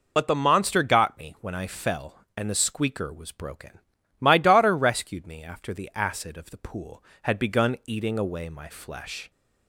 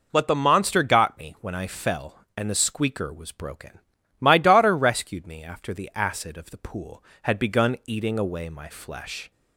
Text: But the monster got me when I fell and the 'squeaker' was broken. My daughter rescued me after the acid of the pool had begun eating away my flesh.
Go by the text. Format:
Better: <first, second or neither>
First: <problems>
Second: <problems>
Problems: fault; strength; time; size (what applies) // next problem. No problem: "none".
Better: second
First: loses the start of "But"; at 0.1 s; 40 ms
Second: none